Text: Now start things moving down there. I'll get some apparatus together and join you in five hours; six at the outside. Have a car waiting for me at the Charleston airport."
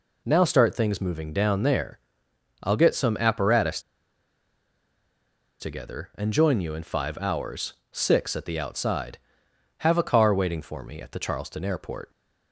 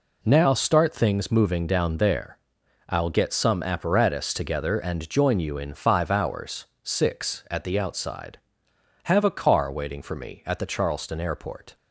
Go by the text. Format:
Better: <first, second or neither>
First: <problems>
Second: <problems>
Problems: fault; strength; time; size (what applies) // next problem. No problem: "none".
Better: second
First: pauses between "apparatus" and "together"; strong; at 3.8 s; 1.7 s long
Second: none